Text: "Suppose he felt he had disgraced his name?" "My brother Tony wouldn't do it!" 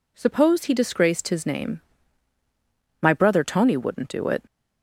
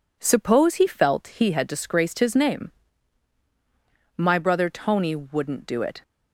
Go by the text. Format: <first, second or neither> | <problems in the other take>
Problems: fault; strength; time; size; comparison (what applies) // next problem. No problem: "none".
second | skips "felt he had"; at 0.7 s